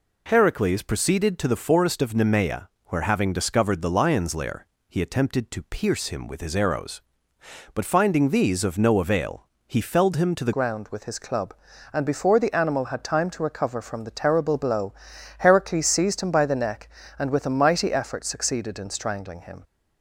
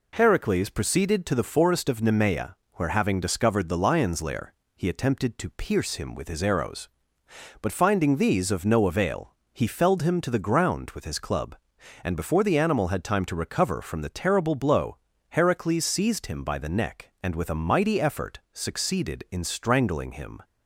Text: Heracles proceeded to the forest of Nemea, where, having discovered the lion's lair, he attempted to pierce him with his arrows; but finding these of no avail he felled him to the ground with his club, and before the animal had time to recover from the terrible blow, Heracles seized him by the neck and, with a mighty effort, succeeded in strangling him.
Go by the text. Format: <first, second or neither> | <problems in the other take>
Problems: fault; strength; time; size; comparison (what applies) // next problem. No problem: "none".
second | pauses between "avail" and "he"; slight; at 9.4 s; 0.22 s long; slight in the second // changes voice at "ground"; from 10.5 s on; 9.1 s long